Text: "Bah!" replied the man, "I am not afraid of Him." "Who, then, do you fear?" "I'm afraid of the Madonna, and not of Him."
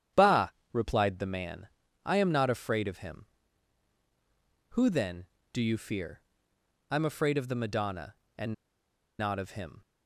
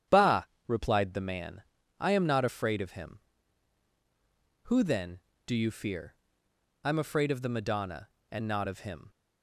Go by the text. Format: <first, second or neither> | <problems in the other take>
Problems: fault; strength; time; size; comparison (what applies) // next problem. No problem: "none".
second | starts louder than the rest; strong; until 1.3 s; 9.5 dB; strong in the second // pauses between "and" and "not"; noticeable; at 8.5 s; 0.66 s long